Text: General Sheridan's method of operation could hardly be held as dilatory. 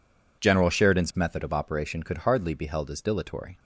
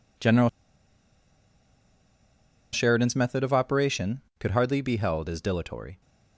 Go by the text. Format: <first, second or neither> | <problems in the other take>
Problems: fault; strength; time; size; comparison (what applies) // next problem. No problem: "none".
first | pauses between "General" and "Sheridan's"; strong; at 0.4 s; 2.2 s long